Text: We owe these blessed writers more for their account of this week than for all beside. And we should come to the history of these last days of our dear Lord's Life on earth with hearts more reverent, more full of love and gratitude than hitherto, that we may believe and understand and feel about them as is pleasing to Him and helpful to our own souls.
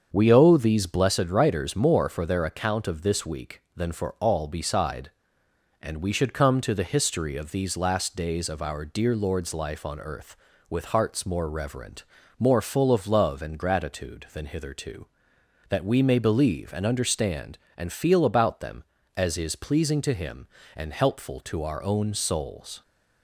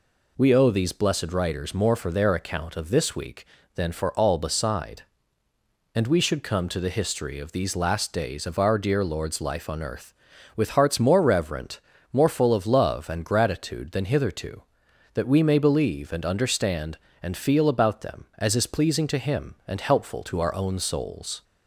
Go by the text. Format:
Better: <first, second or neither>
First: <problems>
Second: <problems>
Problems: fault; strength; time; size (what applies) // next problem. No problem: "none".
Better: second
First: starts louder than the rest; strong; until 1.2 s; 7 dB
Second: none